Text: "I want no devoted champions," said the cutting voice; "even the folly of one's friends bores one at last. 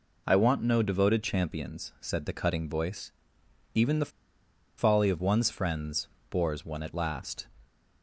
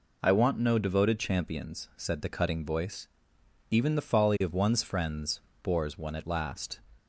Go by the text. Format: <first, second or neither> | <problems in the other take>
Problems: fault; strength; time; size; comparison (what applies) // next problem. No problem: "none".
second | pauses between "the" and "folly"; noticeable; at 4.0 s; 0.69 s long // pauses between "friends" and "bores"; slight; at 6.0 s; 0.22 s long; slight in the second